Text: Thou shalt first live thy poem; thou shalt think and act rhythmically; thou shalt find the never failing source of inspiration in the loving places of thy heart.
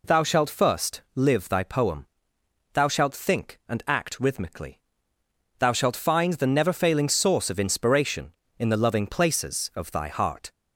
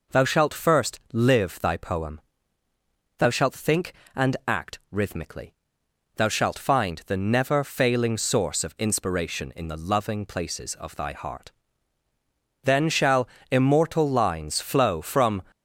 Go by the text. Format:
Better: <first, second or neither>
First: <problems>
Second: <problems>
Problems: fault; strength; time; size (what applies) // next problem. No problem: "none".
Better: first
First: none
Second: goes on to say "Then shall immortal lines flow from"; strong; from 12.6 s on; 2.8 s long